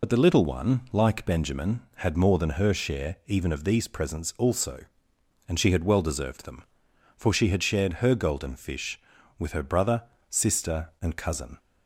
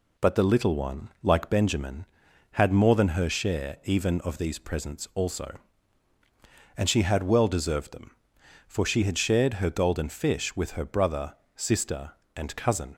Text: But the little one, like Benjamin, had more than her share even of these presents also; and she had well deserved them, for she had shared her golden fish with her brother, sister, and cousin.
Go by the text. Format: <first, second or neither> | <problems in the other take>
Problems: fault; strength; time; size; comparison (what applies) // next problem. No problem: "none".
second | loses the start of "But"; at 0.0 s; 60 ms